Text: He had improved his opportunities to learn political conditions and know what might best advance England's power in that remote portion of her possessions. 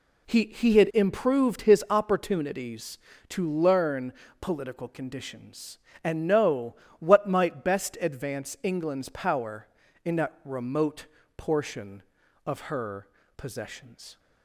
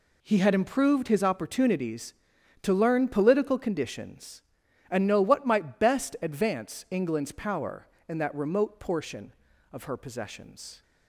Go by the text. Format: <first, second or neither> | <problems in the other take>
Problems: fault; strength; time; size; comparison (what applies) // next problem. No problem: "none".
second | says "He" twice; at 0.4 s // pauses between "learn" and "political"; slight; at 4.1 s; 0.28 s long // pauses between "know" and "what"; slight; at 6.7 s; 0.24 s long // pauses between "remote" and "portion"; slight; at 11.0 s; 0.30 s long // pauses between "her" and "possessions"; slight; at 13.0 s; 0.30 s long